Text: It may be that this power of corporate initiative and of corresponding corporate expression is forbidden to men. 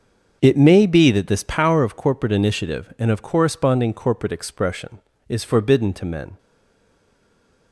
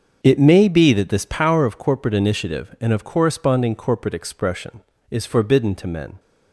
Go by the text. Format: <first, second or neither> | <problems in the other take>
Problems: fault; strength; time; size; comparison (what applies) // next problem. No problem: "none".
second | starts louder than the rest; until 1.4 s; 7 dB; also in the second // stays silent after the last word; noticeable; from 6.3 s on; 1.4 s long